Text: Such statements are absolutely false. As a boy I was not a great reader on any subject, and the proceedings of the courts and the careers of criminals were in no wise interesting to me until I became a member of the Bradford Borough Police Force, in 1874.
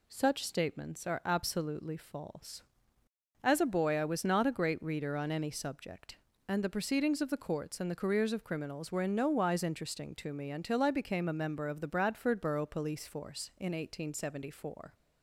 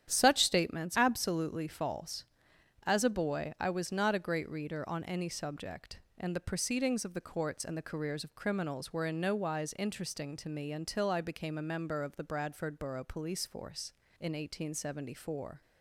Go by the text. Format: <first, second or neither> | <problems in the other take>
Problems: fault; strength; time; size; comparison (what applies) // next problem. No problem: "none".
first | starts louder than the rest; strong; until 1.1 s; 10 dB // skips "are"; at 0.9 s